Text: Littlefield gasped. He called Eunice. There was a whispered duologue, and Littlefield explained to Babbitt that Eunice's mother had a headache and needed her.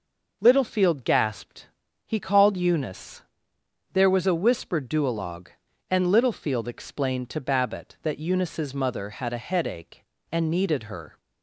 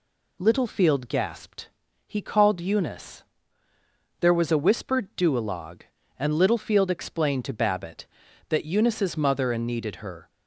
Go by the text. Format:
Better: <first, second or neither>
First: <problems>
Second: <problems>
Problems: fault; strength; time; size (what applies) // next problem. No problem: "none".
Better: first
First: none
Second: skips "had a headache"; at 9.5 s